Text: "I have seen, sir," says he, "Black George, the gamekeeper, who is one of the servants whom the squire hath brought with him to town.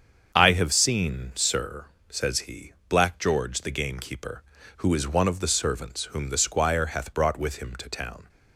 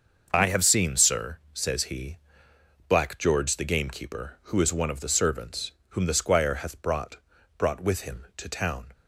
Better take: first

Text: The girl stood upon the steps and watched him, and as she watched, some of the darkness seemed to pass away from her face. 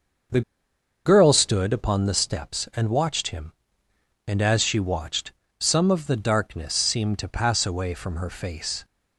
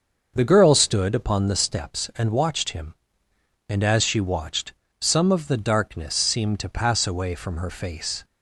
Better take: second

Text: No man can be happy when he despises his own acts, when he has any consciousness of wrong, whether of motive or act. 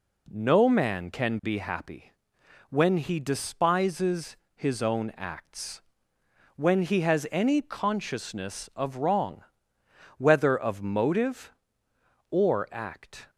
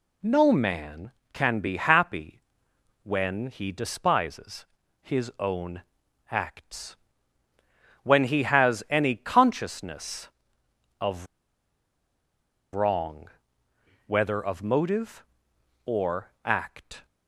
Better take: first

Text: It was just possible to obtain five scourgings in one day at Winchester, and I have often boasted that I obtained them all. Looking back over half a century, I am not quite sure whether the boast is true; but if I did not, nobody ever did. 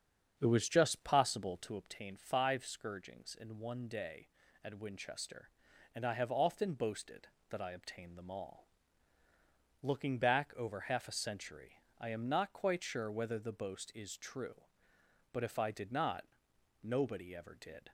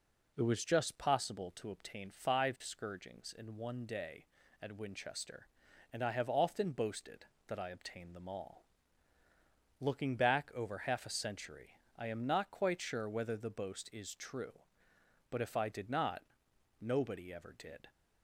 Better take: second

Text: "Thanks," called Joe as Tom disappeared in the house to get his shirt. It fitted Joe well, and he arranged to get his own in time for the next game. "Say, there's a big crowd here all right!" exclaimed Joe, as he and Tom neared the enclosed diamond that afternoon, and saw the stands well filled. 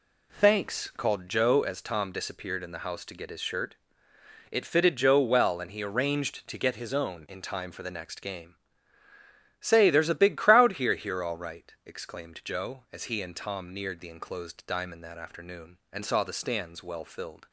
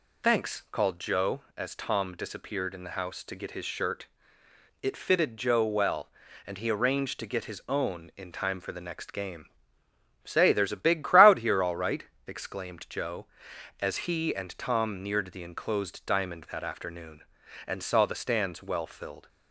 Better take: second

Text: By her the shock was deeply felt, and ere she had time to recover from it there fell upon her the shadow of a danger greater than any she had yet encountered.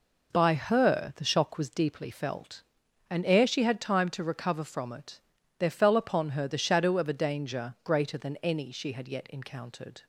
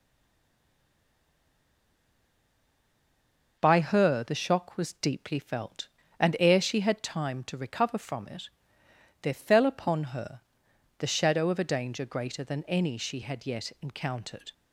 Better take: first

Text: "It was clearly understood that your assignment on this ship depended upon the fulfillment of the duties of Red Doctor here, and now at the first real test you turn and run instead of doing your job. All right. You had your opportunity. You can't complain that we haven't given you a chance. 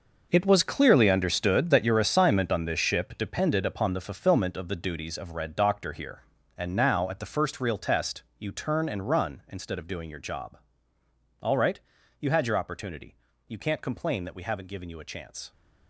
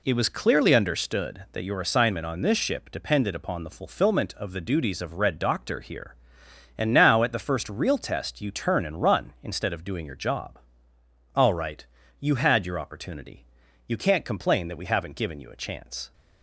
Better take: second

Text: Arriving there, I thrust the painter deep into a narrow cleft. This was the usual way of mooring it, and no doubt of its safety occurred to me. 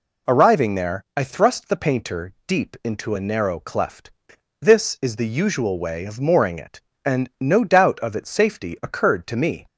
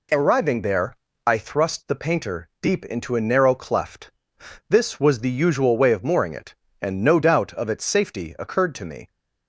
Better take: second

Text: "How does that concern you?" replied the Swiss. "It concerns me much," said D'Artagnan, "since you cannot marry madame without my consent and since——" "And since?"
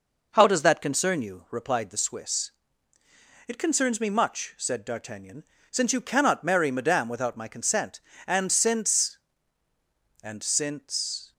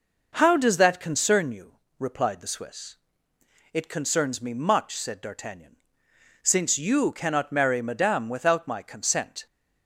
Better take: first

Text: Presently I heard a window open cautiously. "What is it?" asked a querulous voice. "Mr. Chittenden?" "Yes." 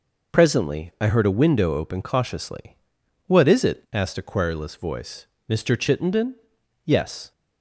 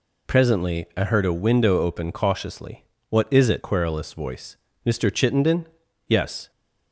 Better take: first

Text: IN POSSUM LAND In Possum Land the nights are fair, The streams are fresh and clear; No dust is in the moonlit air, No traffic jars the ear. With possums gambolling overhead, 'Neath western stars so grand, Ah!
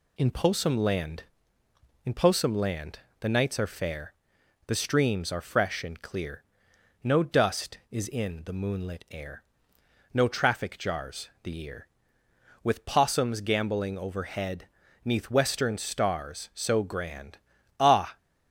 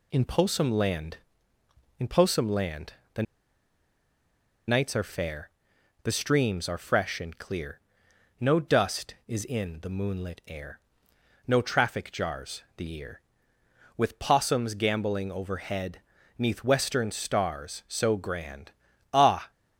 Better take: first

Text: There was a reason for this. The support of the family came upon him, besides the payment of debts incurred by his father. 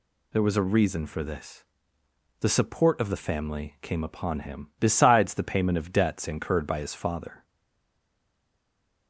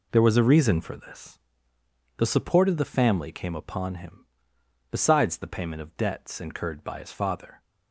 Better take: second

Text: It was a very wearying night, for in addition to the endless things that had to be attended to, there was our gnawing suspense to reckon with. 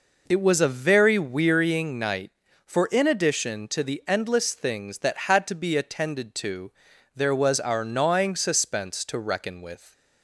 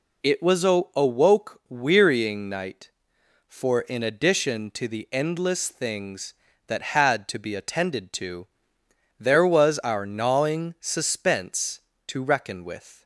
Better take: first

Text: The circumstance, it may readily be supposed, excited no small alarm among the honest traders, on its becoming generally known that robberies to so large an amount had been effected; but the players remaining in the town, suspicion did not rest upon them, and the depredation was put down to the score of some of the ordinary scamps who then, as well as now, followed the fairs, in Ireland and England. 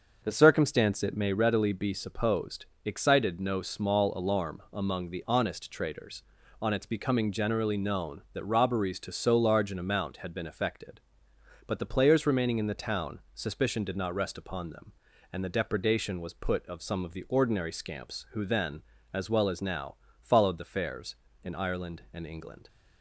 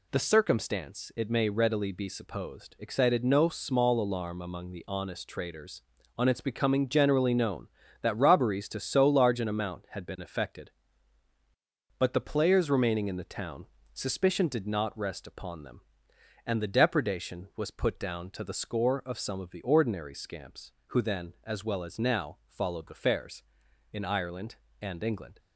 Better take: second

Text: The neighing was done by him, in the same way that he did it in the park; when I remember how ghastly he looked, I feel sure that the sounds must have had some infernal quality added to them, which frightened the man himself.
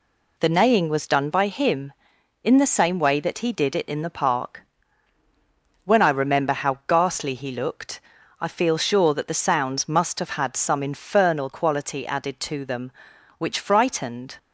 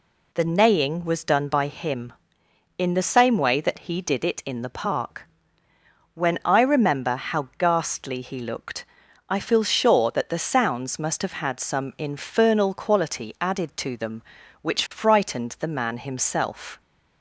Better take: second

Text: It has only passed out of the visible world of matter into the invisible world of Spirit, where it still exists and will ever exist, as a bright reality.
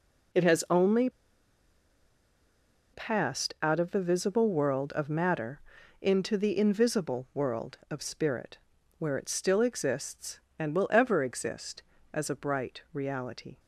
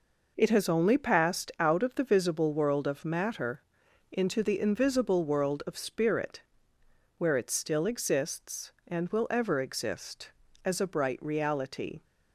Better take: second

